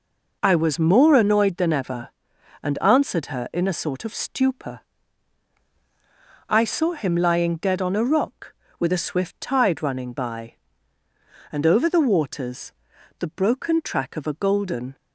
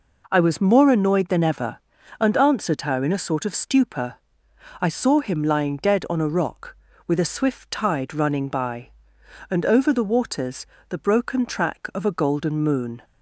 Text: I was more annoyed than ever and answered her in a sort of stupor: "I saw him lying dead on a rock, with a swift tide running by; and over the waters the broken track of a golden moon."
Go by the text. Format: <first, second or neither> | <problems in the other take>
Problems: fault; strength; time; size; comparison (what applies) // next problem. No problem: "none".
second | pauses between "waters" and "the"; noticeable; at 12.7 s; 0.48 s long; slight in the second // stops before "moon"; at 14.9 s